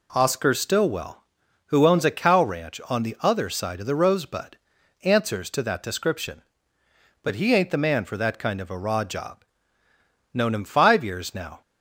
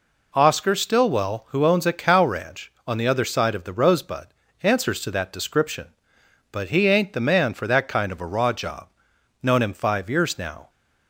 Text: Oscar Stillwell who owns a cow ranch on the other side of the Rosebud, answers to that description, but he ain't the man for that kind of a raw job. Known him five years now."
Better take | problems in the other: neither | none

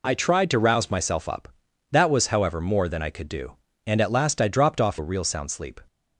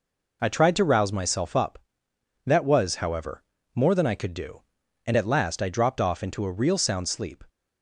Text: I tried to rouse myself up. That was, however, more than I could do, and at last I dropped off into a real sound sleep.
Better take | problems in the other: second | skips "into"; at 4.9 s

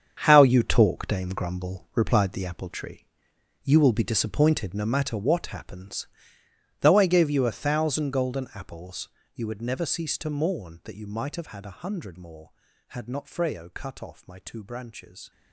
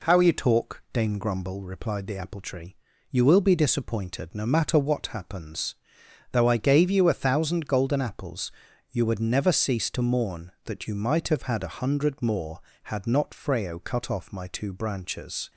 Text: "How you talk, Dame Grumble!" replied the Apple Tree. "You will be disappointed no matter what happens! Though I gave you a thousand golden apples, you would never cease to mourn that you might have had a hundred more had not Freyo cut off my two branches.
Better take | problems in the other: second | gets quieter; strong; throughout; 11.5 dB

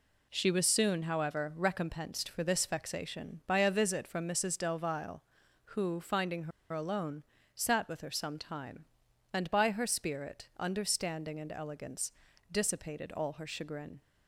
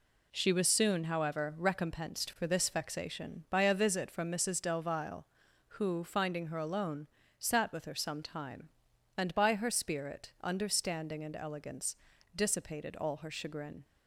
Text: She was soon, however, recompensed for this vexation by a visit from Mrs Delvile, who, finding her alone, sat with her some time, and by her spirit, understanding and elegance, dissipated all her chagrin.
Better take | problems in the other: second | pauses between "her" and "alone"; slight; at 6.5 s; 0.22 s long

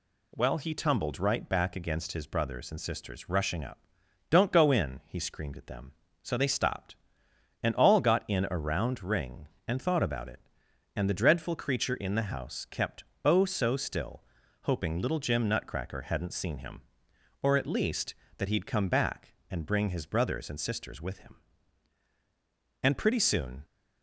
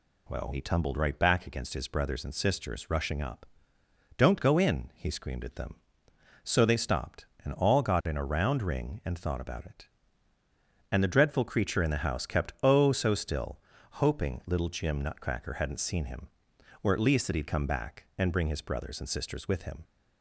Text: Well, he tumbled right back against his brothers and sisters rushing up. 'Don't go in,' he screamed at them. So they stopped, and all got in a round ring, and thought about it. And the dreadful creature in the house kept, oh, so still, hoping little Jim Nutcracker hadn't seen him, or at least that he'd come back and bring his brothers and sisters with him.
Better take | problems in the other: second | goes on to say "And pretty soon"; noticeable; from 22.8 s on; 0.80 s long

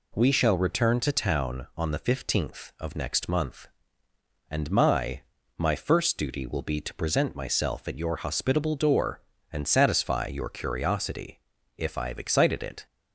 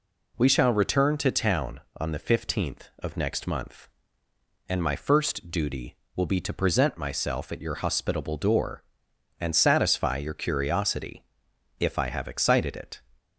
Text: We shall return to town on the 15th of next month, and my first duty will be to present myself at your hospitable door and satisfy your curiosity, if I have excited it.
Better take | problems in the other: second | says "my" twice; at 5.5 s

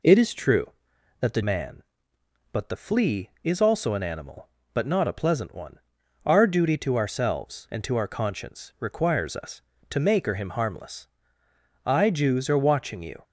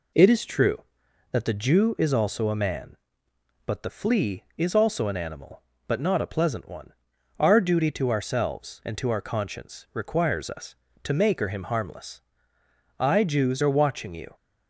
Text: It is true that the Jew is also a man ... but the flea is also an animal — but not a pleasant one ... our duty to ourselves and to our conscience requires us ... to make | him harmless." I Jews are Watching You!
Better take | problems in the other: second | skips "Jew is also a"; at 1.4 s

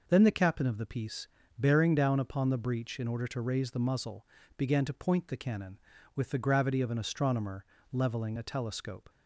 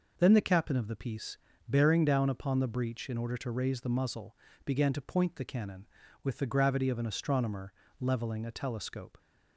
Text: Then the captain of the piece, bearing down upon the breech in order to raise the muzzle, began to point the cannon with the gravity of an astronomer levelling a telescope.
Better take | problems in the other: neither | pauses between "astronomer" and "levelling"; slight; the same in both

